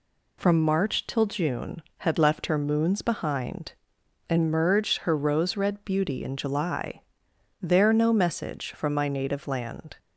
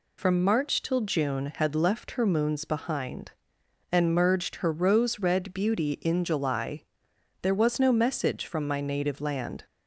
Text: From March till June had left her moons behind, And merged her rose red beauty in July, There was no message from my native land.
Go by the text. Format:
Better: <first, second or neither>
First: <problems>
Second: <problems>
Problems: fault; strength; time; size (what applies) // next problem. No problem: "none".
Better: second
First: skips "was"; at 7.9 s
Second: none